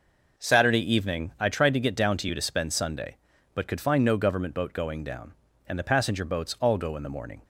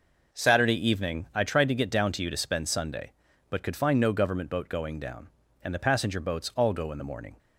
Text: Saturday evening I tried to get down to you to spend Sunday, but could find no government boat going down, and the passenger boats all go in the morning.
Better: neither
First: none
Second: none

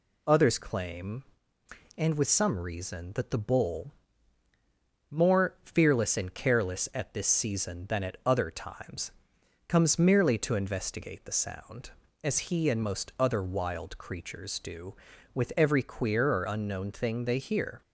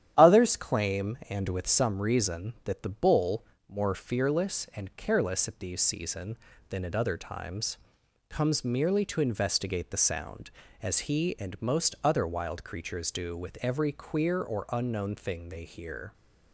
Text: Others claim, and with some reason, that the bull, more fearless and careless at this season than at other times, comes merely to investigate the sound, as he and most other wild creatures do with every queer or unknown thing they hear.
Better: first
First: none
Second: starts louder than the rest; strong; until 1.1 s; 10.5 dB // says "these" for "this"; at 5.5 s

